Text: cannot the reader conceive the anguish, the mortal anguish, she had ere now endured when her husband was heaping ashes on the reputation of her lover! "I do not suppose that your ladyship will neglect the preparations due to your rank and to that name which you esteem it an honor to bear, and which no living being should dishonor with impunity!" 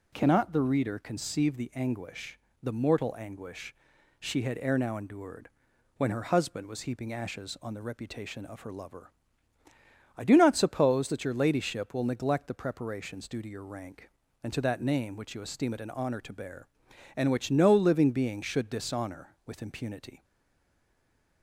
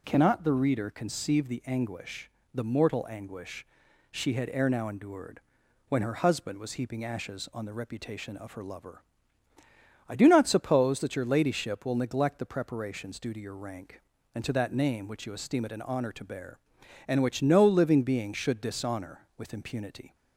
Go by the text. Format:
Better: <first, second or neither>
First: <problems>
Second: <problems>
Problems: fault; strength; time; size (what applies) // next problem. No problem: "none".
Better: second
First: pauses between "endured" and "when"; noticeable; at 5.4 s; 0.48 s long // stays silent after the last word; noticeable; from 20.2 s on; 1.2 s long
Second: pauses between "endured" and "when"; noticeable; at 5.4 s; 0.48 s long